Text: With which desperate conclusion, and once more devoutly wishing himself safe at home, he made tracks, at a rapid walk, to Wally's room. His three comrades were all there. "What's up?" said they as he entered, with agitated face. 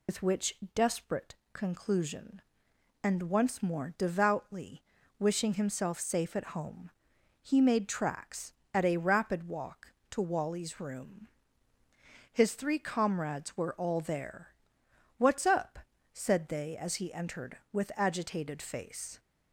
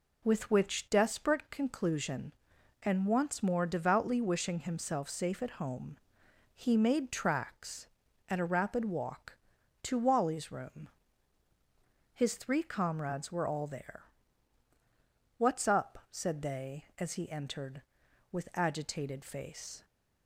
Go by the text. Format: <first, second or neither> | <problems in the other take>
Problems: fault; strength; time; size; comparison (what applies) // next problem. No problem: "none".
second | loses the start of "With"; at 0.0 s; 115 ms // pauses between "which" and "desperate"; slight; at 0.5 s; 0.18 s long // pauses between "desperate" and "conclusion"; slight; at 1.3 s; 0.18 s long // pauses between "devoutly" and "wishing"; at 4.8 s; 0.38 s long